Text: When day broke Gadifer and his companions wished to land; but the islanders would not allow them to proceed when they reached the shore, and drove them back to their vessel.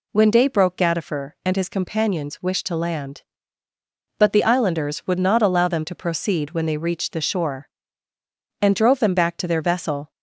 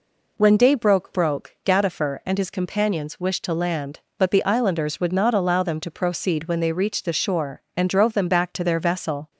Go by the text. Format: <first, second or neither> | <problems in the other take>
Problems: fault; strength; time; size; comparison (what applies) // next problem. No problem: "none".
first | says "broke" twice; at 1.1 s